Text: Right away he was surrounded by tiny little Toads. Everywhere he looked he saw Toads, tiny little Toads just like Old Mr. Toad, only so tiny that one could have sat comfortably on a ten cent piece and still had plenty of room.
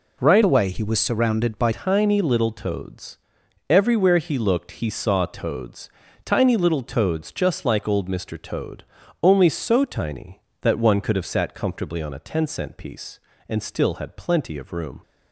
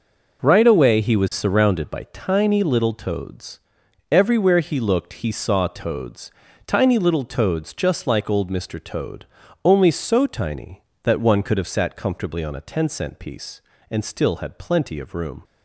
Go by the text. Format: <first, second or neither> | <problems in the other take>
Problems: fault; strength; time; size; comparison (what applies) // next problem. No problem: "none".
second | changes voice from "away" to "by"; from 0.4 to 1.7 s; 1.3 s long